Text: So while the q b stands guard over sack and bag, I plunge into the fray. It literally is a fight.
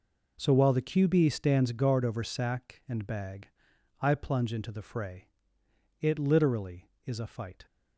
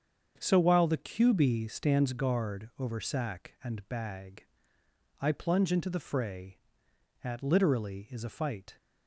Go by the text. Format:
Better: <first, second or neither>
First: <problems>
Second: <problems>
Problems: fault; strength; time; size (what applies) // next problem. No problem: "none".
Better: first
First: none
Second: starts louder than the rest; until 1.3 s; 7 dB // says "At" for "It"; at 7.2 s